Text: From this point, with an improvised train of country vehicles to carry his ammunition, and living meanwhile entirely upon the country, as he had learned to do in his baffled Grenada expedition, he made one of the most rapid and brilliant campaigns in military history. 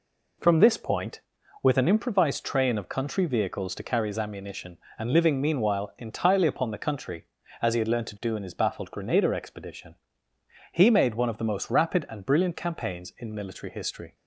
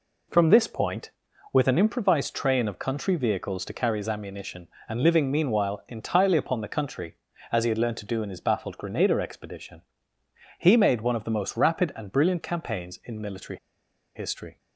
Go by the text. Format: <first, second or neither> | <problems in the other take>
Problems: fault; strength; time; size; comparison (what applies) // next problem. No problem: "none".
first | pauses between "military" and "history"; noticeable; at 13.5 s; 0.57 s long